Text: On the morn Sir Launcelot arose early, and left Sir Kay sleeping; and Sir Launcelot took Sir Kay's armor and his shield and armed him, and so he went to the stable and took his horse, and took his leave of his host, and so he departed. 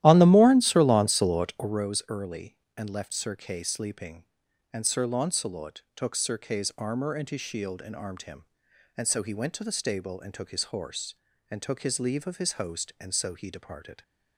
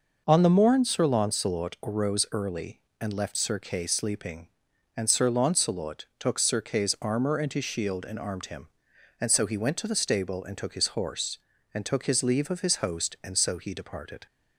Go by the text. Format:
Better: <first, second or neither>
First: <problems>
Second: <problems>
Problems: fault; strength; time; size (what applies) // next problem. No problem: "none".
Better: second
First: starts louder than the rest; strong; until 1.9 s; 13 dB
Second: none